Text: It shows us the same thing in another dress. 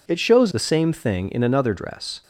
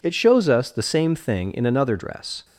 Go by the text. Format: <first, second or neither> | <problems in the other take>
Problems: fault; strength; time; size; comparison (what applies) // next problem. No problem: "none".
second | skips "us"; at 0.5 s